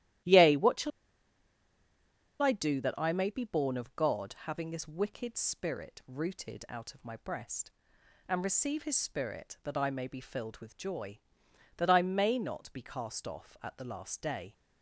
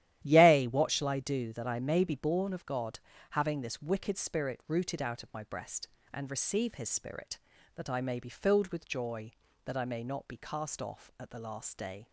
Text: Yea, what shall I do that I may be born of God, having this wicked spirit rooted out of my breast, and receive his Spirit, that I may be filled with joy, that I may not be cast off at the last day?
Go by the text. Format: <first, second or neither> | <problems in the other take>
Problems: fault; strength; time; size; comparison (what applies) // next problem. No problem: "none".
second | starts louder than the rest; strong; until 2.7 s; 13 dB; strong in the second // pauses between "shall" and "I"; strong; at 0.9 s; 1.5 s long